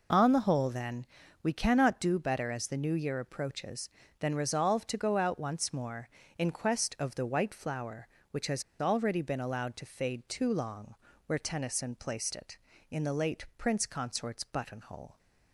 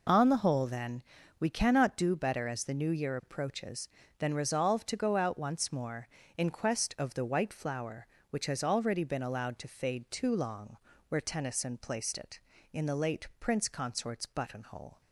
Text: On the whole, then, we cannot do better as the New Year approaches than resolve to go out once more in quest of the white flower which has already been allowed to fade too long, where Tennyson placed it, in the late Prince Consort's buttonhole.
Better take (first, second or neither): second